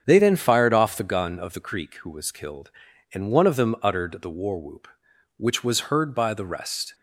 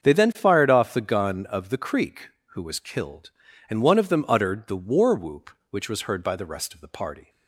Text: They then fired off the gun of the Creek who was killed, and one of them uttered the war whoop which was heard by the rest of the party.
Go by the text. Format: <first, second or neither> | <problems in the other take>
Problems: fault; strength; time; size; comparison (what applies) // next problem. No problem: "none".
second | starts louder than the rest; strong; until 1.0 s; 7.5 dB; also in the second // stops before "of the party"; at 6.9 s